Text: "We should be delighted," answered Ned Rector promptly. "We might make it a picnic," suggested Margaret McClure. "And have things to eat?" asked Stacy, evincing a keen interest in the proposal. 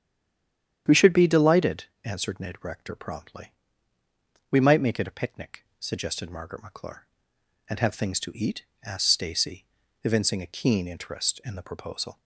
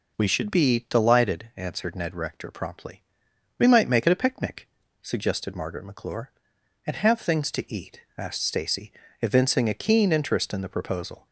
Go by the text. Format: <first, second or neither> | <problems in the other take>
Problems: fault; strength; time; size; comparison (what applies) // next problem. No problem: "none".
second | stays silent before the first word; slight; until 0.8 s; 0.8 s long // starts louder than the rest; strong; until 2.0 s; 9.5 dB